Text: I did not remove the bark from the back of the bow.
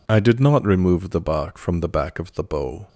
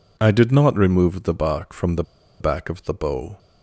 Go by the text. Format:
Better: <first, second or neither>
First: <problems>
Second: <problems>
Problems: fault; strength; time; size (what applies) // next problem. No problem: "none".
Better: first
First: none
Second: pauses between "the" and "back"; at 2.0 s; 0.37 s long